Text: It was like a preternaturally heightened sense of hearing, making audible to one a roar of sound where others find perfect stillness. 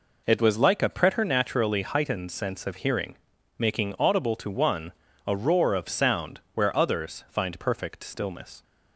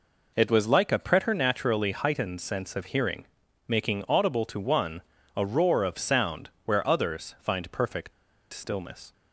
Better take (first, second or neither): first